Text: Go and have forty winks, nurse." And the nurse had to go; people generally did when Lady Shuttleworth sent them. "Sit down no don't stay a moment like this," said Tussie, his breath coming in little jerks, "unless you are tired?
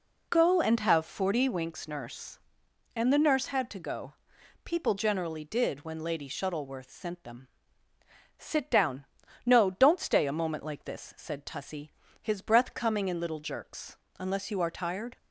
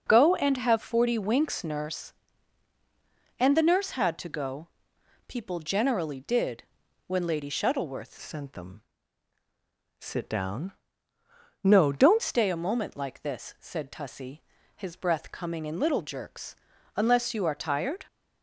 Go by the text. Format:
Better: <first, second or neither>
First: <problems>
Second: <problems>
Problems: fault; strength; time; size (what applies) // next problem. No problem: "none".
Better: first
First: pauses between "down" and "no"; at 9.0 s; 0.40 s long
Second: pauses between "did" and "when"; at 6.6 s; 0.44 s long // changes voice from "sent" to "don't"; from 8.1 to 12.2 s; 4.1 s long // pauses between "down" and "no"; noticeable; at 10.7 s; 0.90 s long